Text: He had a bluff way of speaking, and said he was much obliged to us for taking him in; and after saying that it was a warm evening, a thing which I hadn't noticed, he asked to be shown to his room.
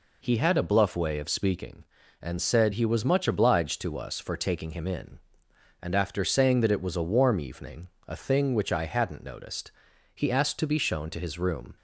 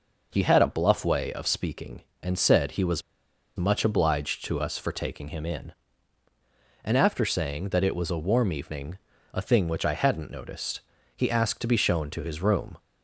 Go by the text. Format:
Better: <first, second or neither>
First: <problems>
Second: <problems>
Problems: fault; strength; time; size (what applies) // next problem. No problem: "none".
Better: first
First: none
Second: pauses between "was" and "much"; noticeable; at 3.0 s; 0.55 s long